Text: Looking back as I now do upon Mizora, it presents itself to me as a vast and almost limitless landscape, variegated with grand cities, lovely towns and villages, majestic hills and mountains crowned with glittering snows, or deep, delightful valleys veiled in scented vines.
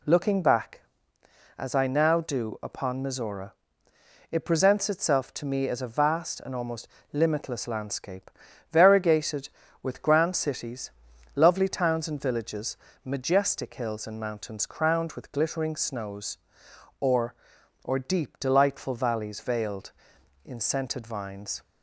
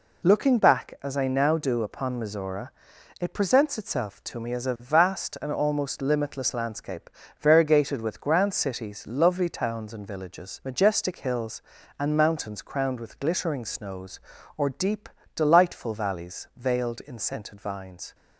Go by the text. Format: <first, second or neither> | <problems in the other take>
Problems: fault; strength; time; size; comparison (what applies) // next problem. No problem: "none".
second | pauses between "almost" and "limitless"; slight; at 6.8 s; 0.24 s long // says "or" twice; at 17.8 s